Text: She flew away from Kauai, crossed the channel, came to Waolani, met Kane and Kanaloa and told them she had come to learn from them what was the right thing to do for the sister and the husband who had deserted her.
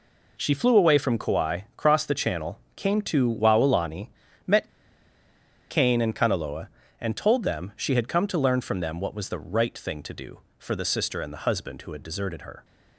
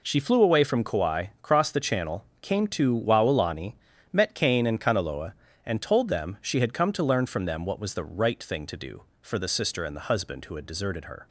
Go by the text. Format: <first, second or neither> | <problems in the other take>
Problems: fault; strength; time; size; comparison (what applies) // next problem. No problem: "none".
second | pauses between "met" and "Kane"; at 4.6 s; 1.0 s long